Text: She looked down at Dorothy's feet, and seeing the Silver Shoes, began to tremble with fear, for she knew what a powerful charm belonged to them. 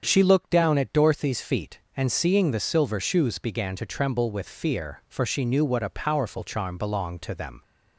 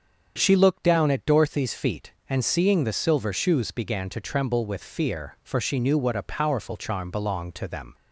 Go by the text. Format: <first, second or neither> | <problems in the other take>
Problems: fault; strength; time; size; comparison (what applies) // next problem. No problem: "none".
neither | starts louder than the rest; strong; the same in both